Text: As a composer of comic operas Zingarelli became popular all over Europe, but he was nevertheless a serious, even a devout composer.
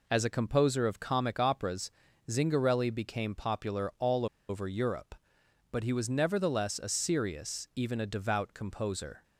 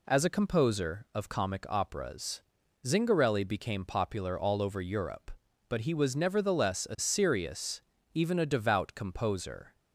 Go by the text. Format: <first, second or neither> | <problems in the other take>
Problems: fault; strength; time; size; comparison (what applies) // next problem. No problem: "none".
second | pauses between "operas" and "Zingarelli"; at 1.8 s; 0.40 s long; also in the second // pauses between "all" and "over"; slight; at 4.2 s; 0.23 s long